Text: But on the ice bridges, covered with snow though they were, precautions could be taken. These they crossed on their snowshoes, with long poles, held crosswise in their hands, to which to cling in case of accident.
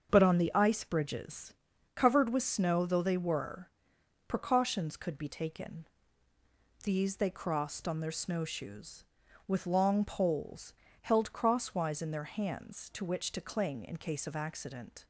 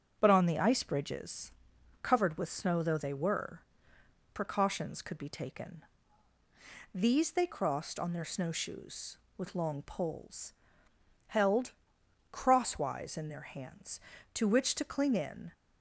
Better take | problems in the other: first | starts louder than the rest; strong; until 1.2 s; 7.5 dB; also in the first // pauses between "held" and "crosswise"; noticeable; at 11.7 s; 0.58 s long // stops before "case of accident"; at 15.5 s

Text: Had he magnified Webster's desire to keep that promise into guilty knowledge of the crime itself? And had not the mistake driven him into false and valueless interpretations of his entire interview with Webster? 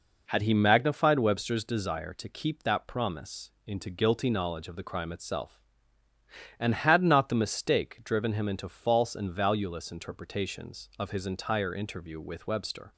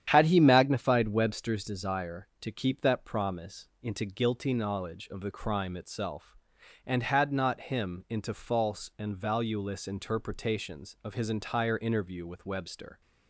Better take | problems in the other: first | starts louder than the rest; strong; until 1.0 s; 9.5 dB // pauses between "promise" and "into"; slight; at 3.6 s; 0.16 s long // skips "the mistake driven"; at 7.6 s

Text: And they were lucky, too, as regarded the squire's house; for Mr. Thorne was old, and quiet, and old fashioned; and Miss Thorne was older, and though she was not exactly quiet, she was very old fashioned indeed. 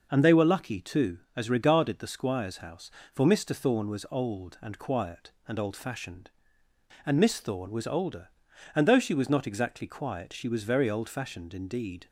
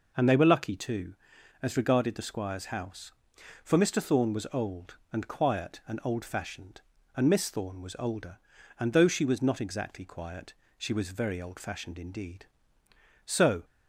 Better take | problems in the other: first | goes on to say "So"; slight; from 13.2 s on; 0.40 s long

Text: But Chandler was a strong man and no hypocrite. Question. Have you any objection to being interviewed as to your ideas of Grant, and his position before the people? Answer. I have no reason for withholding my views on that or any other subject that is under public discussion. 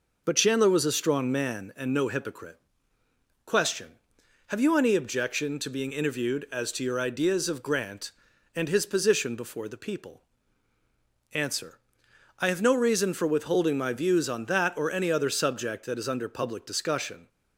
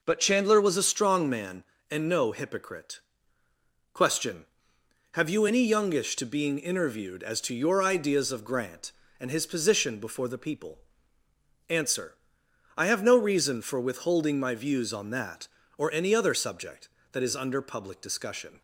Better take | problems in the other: first | says "youngish" for "objection"; at 5.6 s

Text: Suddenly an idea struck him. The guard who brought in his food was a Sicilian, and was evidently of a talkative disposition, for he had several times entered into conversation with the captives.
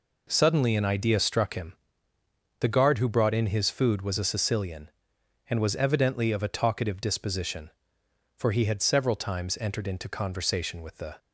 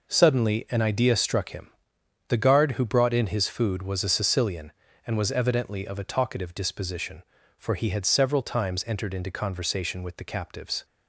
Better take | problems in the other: second | stops before "captives"; at 11.1 s

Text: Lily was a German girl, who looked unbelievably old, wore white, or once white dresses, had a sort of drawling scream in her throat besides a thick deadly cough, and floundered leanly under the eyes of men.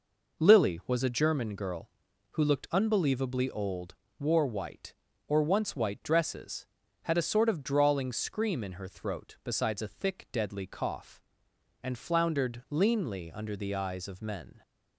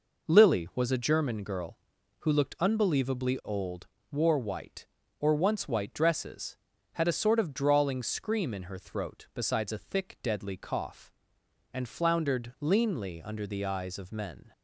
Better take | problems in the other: neither | none

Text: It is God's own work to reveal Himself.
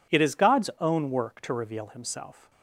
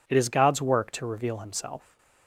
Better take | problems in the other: first | skips "own"; at 0.6 s

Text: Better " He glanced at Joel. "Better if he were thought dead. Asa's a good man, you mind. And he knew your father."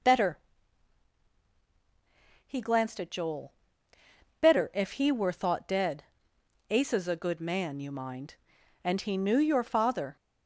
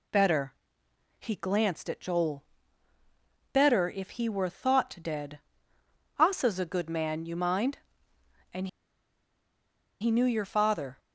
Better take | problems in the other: first | pauses between "And" and "he"; strong; at 8.6 s; 1.3 s long

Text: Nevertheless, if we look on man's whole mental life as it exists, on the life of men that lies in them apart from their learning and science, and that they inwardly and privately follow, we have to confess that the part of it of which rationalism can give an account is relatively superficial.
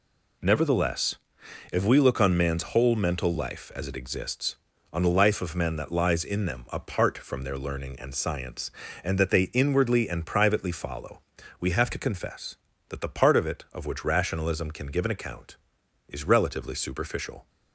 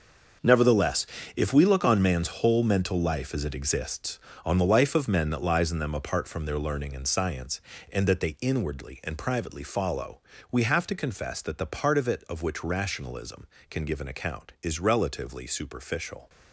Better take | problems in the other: first | gets quieter; strong; throughout; 11 dB

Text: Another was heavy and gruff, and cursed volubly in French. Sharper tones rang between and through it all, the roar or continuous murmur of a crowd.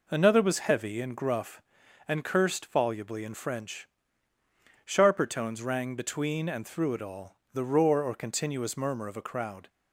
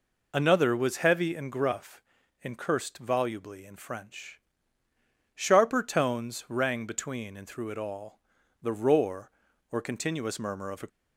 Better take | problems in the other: first | stops before "crowd"; at 10.8 s

